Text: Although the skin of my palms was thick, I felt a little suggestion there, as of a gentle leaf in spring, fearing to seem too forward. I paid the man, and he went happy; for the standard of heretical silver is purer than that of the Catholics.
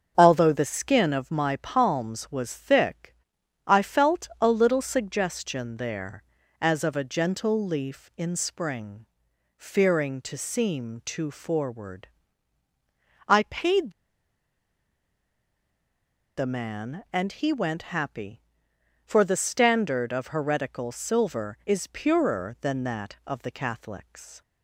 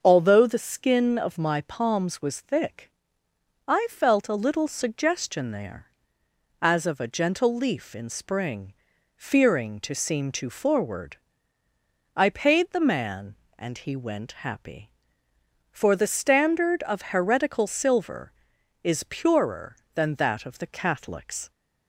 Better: second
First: starts louder than the rest; until 1.1 s; 7 dB // pauses between "paid" and "the"; strong; at 13.9 s; 2.4 s long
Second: starts louder than the rest; until 1.0 s; 6.5 dB

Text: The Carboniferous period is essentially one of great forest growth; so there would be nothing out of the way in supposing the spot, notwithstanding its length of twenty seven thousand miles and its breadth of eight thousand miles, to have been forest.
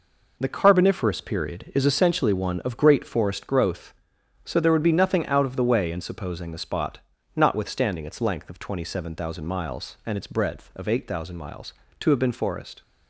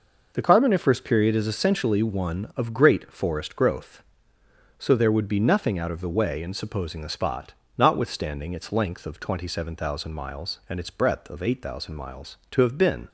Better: first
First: none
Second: stops before "forest"; at 13.0 s

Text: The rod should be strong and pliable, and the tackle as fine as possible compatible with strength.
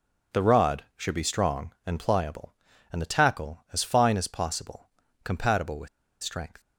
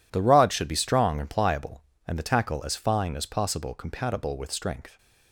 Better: second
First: pauses between "possible" and "compatible"; slight; at 4.8 s; 0.36 s long // pauses between "with" and "strength"; slight; at 5.8 s; 0.35 s long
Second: none

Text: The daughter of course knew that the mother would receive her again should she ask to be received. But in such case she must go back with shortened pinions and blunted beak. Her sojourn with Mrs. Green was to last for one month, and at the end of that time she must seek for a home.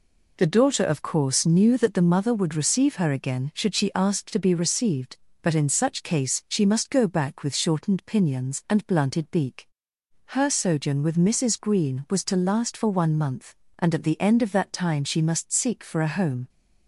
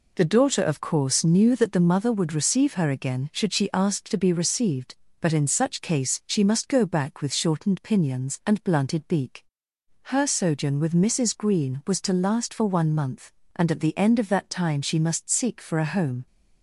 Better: neither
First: none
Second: none

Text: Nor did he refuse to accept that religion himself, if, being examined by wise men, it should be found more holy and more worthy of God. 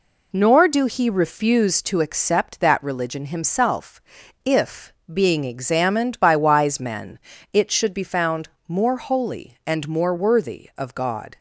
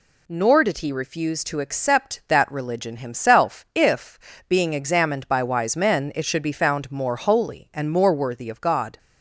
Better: second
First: says "do" for "did"; at 0.6 s // pauses between "found" and "more"; slight; at 8.4 s; 0.20 s long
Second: none

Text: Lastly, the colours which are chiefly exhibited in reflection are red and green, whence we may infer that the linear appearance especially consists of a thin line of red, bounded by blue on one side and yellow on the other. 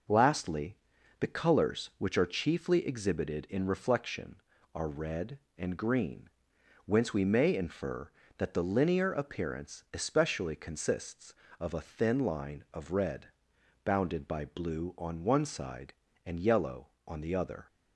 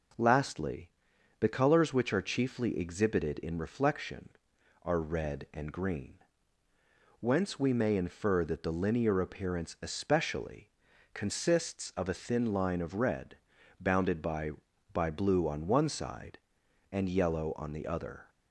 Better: first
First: none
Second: pauses between "especially" and "consists"; noticeable; at 10.6 s; 0.46 s long // says "by" twice; at 14.9 s

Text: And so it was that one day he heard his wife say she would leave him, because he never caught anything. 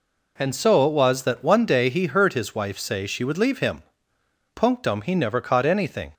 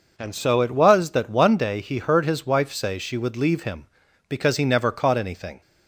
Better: second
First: says "punctum" for "because"; at 4.5 s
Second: none

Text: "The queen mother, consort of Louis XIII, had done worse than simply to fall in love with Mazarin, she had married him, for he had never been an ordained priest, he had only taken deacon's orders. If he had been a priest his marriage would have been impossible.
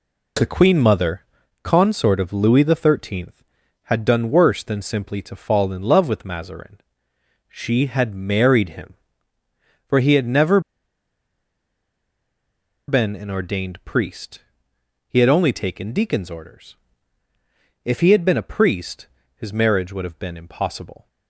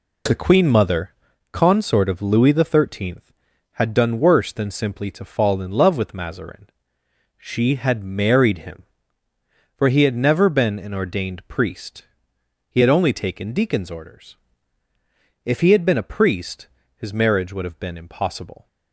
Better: second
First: pauses between "never" and "been"; strong; at 10.5 s; 2.2 s long // pauses between "priest" and "his"; slight; at 19.0 s; 0.28 s long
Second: pauses between "priest" and "his"; slight; at 16.6 s; 0.28 s long

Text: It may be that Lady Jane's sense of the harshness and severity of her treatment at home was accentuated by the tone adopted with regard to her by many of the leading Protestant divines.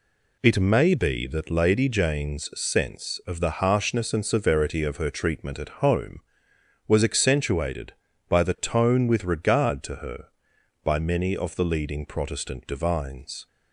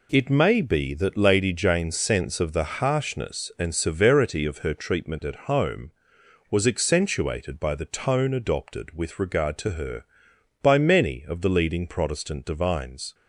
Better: second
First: skips "adopted"; at 9.0 s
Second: none

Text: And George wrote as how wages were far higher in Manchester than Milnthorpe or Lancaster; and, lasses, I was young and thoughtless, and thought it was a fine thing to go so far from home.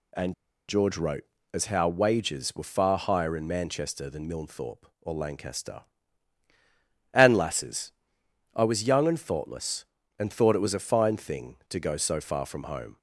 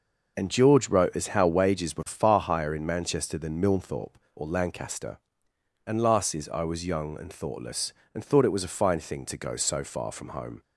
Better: second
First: pauses between "And" and "George"; slight; at 0.3 s; 0.35 s long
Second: none

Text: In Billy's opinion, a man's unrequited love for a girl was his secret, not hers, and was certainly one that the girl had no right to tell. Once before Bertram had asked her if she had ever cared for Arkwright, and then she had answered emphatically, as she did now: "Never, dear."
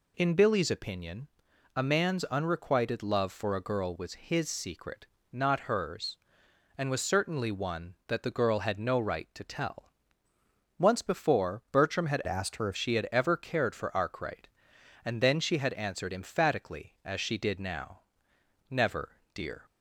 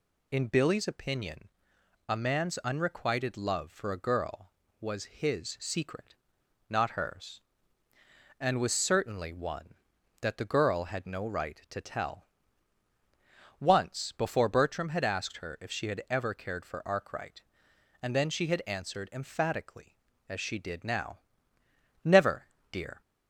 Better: second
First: changes voice from "asked" to "if"; from 12.2 to 12.7 s; 0.5 s long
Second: none

